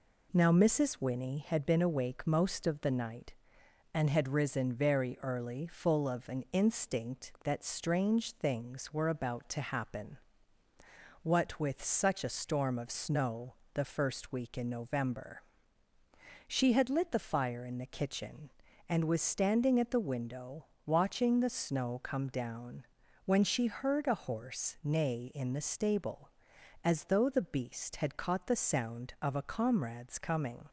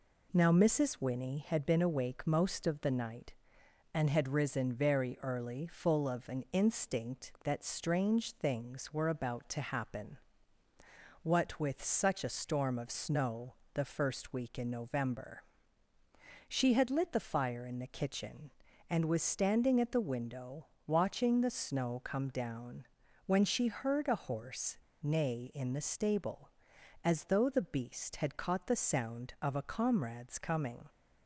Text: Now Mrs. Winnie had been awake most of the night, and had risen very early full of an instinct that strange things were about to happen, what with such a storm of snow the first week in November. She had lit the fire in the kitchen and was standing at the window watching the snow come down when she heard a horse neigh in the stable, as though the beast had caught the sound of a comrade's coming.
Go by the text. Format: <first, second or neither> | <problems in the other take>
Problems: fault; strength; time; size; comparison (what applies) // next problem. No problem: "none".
first | pauses between "snow" and "the"; slight; at 13.5 s; 0.20 s long; slight in the first // pauses between "window" and "watching"; slight; at 20.6 s; 0.20 s long; slight in the first // pauses between "down" and "when"; at 22.8 s; 0.42 s long; also in the first // pauses between "horse" and "neigh"; slight; at 24.7 s; 0.26 s long